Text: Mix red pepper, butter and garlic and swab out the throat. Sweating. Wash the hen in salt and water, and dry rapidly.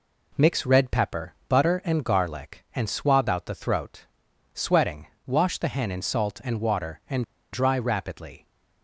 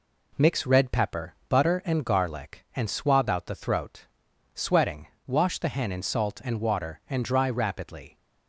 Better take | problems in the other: second | pauses between "and" and "dry"; slight; at 7.2 s; 0.29 s long

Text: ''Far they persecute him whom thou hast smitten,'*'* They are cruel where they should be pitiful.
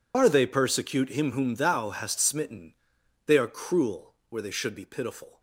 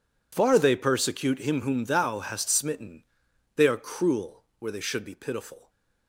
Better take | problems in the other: second | loses the start of "Far"; at 0.1 s; 120 ms

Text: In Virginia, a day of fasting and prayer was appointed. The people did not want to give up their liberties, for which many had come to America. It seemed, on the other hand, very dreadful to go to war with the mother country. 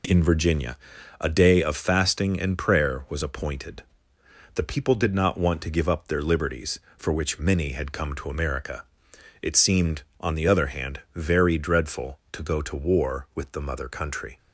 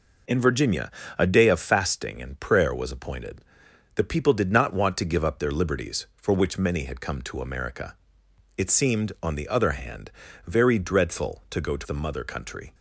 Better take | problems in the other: first | skips "war with"; at 11.8 s

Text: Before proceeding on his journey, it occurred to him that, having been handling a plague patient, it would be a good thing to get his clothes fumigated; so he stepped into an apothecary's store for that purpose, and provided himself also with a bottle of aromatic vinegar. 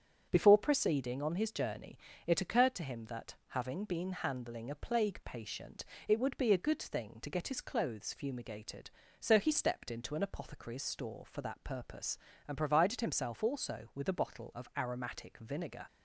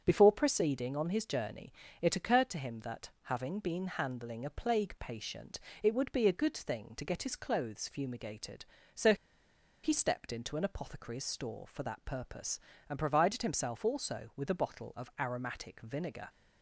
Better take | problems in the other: first | starts louder than the rest; strong; until 1.0 s; 8 dB; strong in the first // pauses between "so" and "he"; noticeable; at 9.1 s; 0.69 s long

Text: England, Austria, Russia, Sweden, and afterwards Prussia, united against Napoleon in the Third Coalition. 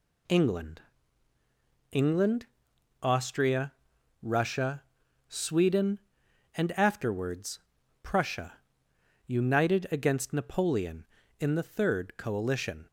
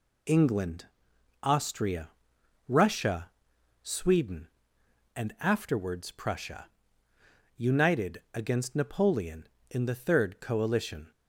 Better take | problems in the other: second | says "England" twice; at 1.9 s // pauses between "afterwards" and "Prussia"; at 7.5 s; 0.42 s long

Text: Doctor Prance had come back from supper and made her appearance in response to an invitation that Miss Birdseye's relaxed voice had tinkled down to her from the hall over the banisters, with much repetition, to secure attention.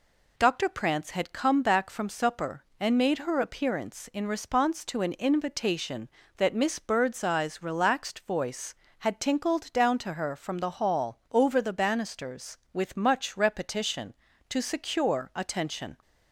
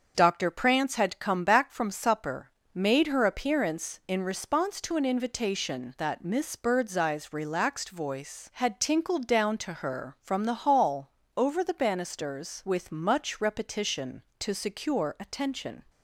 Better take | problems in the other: first | starts louder than the rest; until 1.1 s; 6.5 dB // skips "and"; at 2.6 s // pauses between "hall" and "over"; slight; at 11.0 s; 0.28 s long

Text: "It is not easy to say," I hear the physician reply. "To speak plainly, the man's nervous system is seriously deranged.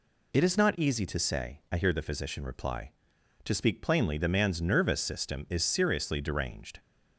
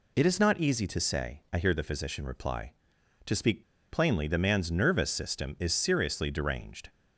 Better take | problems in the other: first | pauses between "speak" and "plainly"; slight; at 3.6 s; 0.28 s long

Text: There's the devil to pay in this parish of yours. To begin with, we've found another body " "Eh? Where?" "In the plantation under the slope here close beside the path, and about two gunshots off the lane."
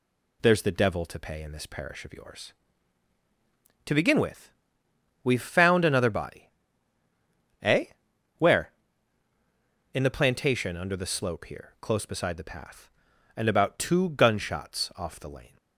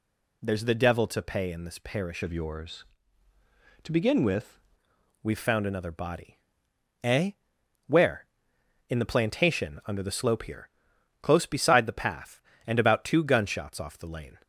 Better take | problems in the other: first | changes voice from "of" to "with"; from 2.2 to 4.5 s; 2.3 s long // pauses between "here" and "close"; noticeable; at 10.6 s; 0.52 s long

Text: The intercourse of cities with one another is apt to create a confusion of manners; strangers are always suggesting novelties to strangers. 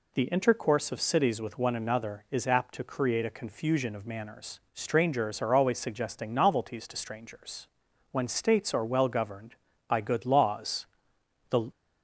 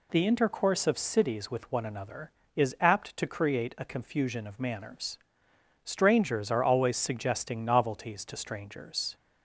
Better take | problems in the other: second | goes on to say "When states are well governed by good laws the"; strong; from 8.1 s on; 3.6 s long

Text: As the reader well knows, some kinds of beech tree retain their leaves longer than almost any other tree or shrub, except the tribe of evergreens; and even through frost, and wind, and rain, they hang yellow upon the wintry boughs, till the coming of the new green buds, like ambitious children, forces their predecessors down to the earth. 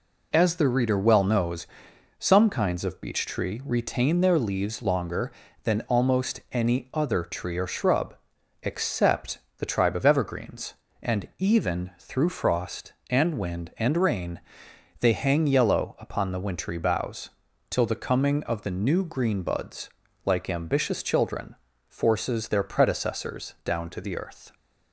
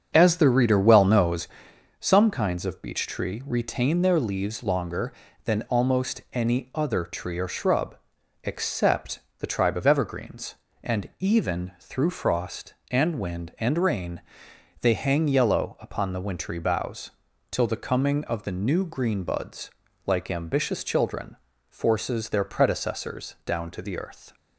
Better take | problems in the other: first | starts louder than the rest; until 1.6 s; 7 dB // pauses between "except" and "the"; slight; at 9.2 s; 0.18 s long; slight in the first

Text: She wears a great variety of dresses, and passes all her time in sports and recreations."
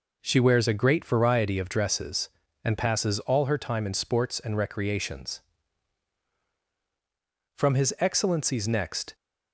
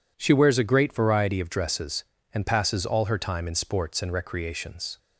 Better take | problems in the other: second | goes on to say "From his excellency's next"; from 7.5 s on; 1.5 s long

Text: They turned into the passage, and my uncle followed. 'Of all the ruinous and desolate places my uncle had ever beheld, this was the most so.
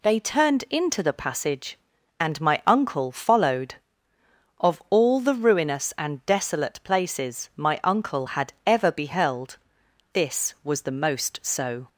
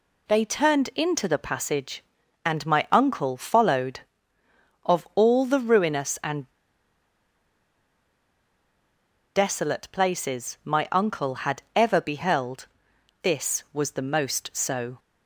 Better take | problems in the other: first | pauses between "and" and "desolate"; strong; at 6.4 s; 2.8 s long

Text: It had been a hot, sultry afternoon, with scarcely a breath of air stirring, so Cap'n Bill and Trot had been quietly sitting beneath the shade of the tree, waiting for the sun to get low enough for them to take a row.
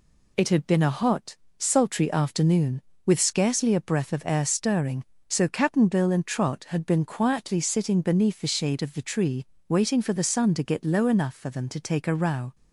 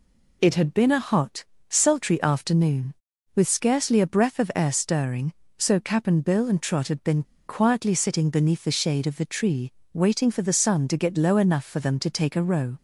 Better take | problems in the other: first | pauses between "been" and "quietly"; slight; at 7.2 s; 0.24 s long

